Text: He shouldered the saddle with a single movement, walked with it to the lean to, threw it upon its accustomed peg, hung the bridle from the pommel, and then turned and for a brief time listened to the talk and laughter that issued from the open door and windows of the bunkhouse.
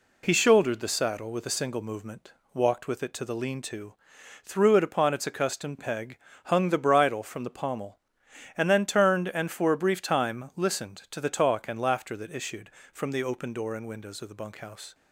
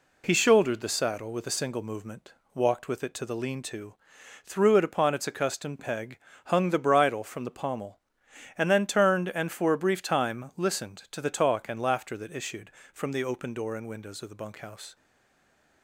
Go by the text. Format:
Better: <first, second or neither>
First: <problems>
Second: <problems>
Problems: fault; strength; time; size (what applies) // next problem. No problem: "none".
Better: first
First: none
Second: stays silent after the last word; slight; from 14.9 s on; 0.9 s long